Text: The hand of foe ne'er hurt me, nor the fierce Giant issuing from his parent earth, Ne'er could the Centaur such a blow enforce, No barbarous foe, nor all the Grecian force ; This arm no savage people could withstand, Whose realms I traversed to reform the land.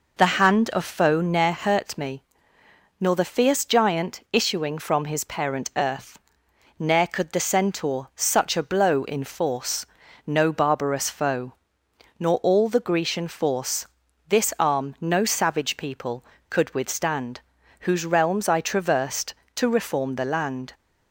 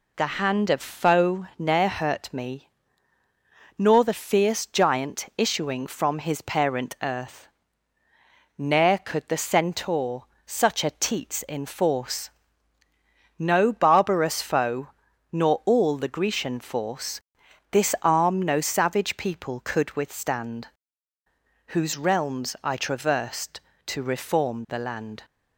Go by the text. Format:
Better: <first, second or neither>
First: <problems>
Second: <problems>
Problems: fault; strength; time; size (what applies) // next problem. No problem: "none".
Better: first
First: none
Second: pauses between "Centaur" and "such"; slight; at 10.2 s; 0.20 s long // says "teats" for "blow"; at 10.9 s